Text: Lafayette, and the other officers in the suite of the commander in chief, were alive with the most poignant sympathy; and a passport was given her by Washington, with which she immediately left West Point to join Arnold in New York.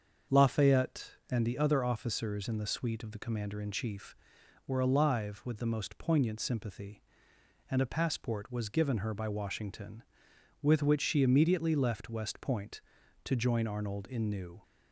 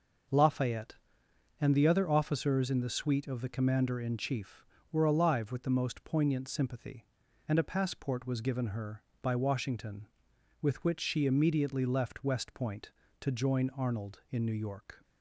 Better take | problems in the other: second | starts louder than the rest; until 1.5 s; 7 dB; noticeable in the second // stops before "York"; at 14.6 s

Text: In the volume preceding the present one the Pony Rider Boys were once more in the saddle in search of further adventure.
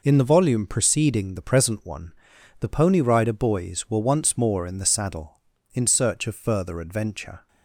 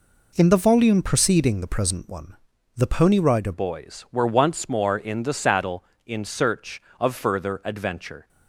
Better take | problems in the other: first | pauses between "one" and "the"; at 2.3 s; 0.40 s long; noticeable in the first // changes voice at "Boys"; from 3.5 s on; 4.7 s long

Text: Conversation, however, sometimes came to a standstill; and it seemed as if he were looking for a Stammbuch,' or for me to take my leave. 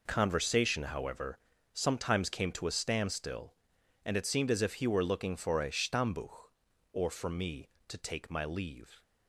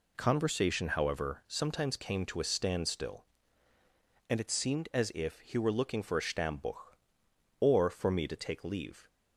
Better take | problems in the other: first | skips "my"; at 8.6 s

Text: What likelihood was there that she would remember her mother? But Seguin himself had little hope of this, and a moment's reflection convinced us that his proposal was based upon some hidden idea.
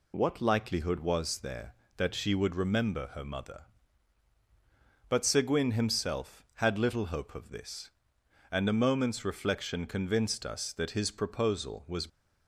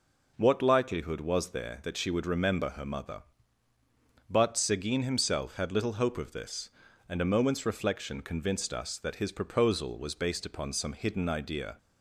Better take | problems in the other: second | stops before "based upon some hidden idea"; at 12.0 s

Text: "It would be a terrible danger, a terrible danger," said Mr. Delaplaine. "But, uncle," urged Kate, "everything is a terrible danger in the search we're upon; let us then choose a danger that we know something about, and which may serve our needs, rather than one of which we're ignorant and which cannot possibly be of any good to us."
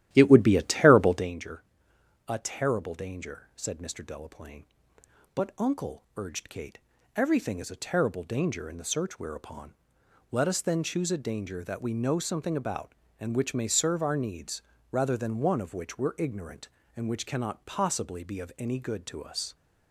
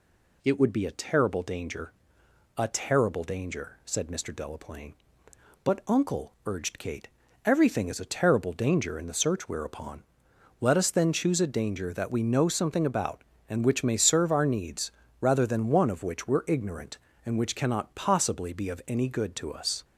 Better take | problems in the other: second | starts louder than the rest; strong; until 1.4 s; 12.5 dB

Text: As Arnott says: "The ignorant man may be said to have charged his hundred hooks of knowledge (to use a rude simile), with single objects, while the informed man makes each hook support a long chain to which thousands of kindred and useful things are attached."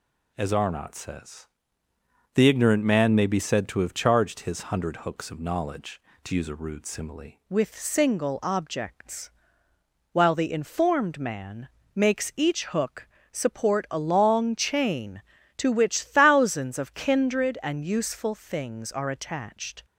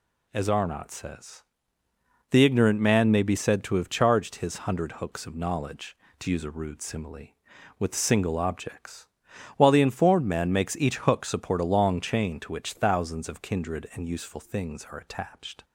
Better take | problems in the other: second | changes voice at "with"; from 7.4 s on; 12.4 s long // pauses between "man" and "makes"; slight; at 11.6 s; 0.26 s long // pauses between "hook" and "support"; slight; at 13.0 s; 0.24 s long

